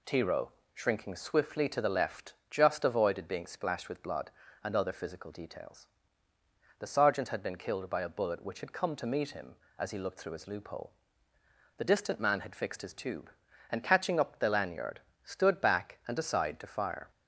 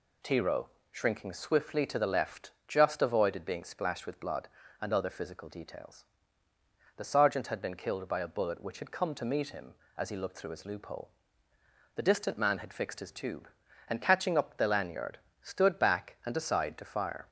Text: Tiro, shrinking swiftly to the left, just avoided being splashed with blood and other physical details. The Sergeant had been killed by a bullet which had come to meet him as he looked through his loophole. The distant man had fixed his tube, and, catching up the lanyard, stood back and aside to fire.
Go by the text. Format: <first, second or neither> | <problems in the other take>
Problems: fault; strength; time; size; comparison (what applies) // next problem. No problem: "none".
neither | none